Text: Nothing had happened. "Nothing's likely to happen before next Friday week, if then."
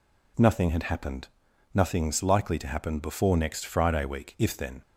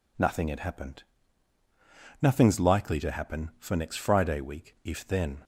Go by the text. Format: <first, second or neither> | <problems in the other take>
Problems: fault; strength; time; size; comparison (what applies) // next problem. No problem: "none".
first | says "for" for "before"; at 3.5 s